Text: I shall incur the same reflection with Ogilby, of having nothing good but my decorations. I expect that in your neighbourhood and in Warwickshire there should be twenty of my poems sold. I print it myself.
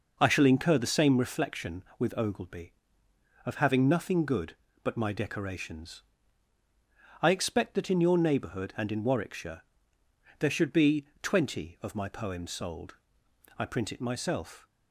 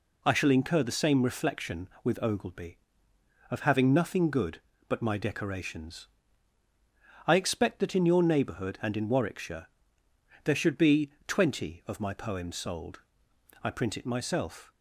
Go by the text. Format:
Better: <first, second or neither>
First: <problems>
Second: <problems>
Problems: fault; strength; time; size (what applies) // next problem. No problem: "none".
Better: second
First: starts louder than the rest; noticeable; until 1.3 s; 5.5 dB // pauses between "Warwickshire" and "there"; noticeable; at 9.6 s; 0.78 s long // pauses between "be" and "twenty"; slight; at 11.0 s; 0.16 s long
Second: pauses between "Warwickshire" and "there"; noticeable; at 9.6 s; 0.78 s long // pauses between "be" and "twenty"; slight; at 11.1 s; 0.16 s long